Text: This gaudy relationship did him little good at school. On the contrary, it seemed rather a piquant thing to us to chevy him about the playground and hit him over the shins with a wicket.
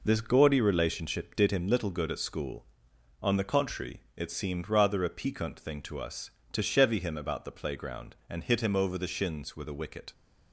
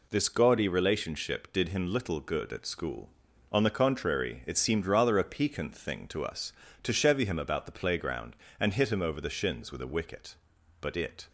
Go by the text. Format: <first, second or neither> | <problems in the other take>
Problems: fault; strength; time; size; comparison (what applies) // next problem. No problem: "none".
first | goes on to say "But it"; slight; from 10.8 s on; 0.48 s long